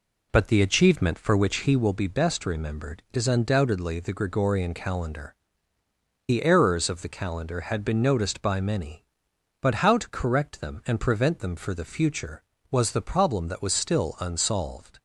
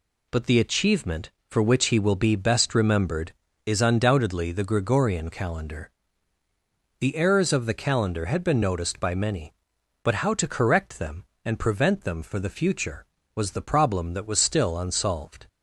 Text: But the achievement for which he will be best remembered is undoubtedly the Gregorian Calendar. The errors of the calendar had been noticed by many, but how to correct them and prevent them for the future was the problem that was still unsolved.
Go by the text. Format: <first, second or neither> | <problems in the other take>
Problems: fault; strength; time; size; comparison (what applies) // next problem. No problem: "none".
second | starts louder than the rest; slight; until 2.0 s; 3 dB